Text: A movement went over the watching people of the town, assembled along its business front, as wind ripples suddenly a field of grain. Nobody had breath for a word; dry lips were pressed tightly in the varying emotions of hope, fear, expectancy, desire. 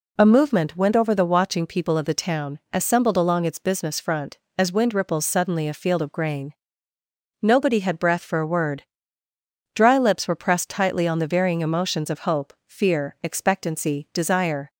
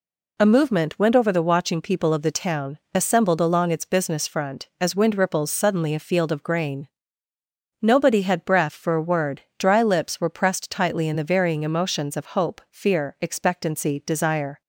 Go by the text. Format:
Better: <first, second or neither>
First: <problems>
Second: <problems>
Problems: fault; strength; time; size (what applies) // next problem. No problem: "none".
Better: second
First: says "on" for "in"; at 11.0 s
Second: none